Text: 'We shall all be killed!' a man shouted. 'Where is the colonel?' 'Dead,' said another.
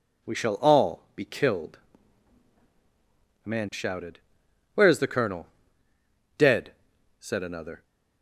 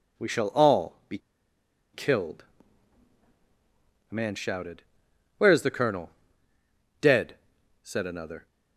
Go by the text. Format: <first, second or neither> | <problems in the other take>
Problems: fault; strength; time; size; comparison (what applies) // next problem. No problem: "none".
first | pauses between "be" and "killed"; noticeable; at 1.1 s; 0.75 s long